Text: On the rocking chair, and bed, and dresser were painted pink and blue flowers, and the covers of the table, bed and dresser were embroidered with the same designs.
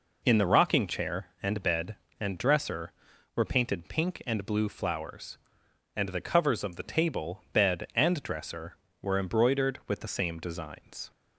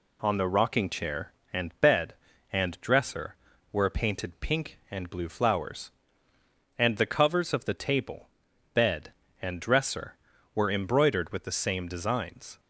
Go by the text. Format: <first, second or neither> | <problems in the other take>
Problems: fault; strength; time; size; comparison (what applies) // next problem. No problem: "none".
second | says "In" for "On"; at 0.2 s